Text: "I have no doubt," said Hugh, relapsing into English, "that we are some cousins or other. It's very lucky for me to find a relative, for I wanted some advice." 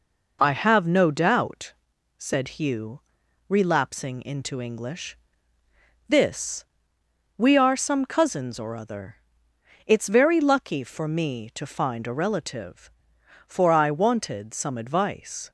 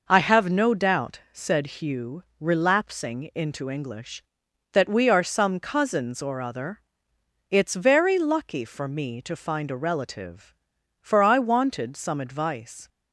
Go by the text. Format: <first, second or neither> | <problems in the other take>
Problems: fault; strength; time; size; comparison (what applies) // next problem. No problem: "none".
second | says "this" for "that"; at 6.0 s